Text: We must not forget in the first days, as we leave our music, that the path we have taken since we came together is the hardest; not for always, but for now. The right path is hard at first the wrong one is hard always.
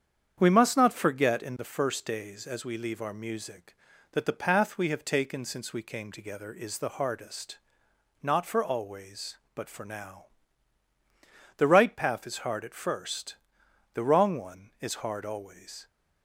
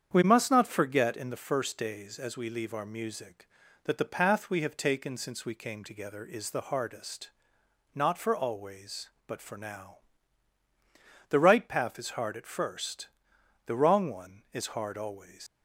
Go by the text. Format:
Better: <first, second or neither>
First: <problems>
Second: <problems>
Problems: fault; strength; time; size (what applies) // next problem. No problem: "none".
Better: first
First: starts louder than the rest; strong; until 1.3 s; 8 dB // pauses between "first" and "the"; noticeable; at 13.3 s; 0.56 s long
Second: starts louder than the rest; strong; until 1.1 s; 8 dB // pauses between "first" and "the"; noticeable; at 13.0 s; 0.56 s long // leaves "always" unfinished; at 15.4 s; 120 ms